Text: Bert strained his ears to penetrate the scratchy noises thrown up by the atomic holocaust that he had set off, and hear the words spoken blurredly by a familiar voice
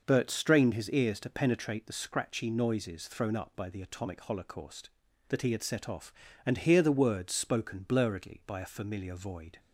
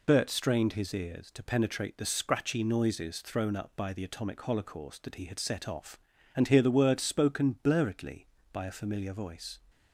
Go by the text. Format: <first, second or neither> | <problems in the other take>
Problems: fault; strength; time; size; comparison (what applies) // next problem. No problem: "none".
second | says "void" for "voice"; at 9.1 s